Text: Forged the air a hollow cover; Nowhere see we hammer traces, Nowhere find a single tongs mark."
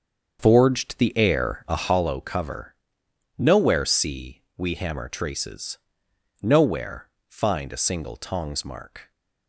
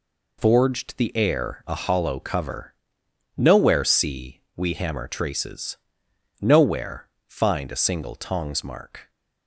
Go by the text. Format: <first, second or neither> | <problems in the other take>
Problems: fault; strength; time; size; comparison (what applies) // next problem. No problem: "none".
second | starts louder than the rest; until 2.2 s; 7 dB // pauses between "see" and "we"; slight; at 4.4 s; 0.16 s long; slight in the second // pauses between "Nowhere" and "find"; slight; at 7.1 s; 0.18 s long; slight in the second